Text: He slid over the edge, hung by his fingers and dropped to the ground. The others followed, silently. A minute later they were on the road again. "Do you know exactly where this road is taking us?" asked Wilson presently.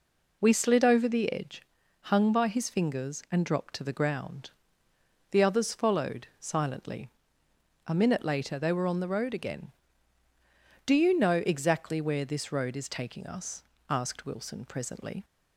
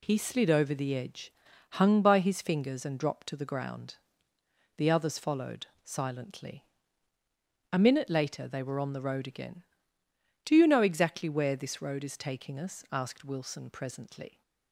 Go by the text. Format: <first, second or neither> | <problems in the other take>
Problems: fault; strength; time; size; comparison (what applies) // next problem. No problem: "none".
second | says "We" for "He"; at 0.4 s